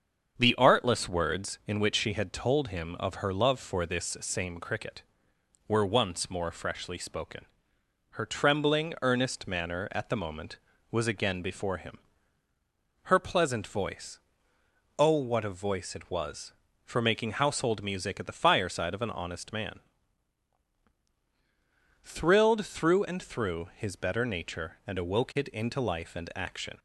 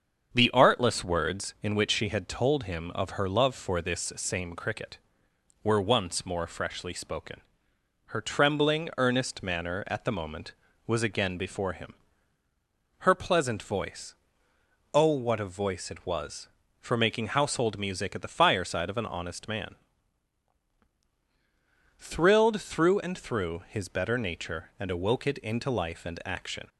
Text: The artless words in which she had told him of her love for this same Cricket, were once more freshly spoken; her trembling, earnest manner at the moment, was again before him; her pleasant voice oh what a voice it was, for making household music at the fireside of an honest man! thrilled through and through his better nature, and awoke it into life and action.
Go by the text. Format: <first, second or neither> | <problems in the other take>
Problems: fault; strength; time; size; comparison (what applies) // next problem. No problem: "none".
neither | starts louder than the rest; strong; the same in both // pauses between "voice" and "oh"; noticeable; the same in both